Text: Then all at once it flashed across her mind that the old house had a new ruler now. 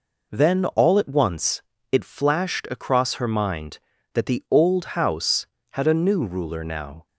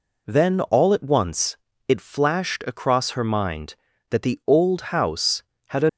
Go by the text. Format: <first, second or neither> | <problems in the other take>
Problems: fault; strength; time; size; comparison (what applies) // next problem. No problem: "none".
first | pauses between "once" and "it"; slight; at 1.5 s; 0.30 s long; slight in the first // stops before "new ruler now"; at 5.8 s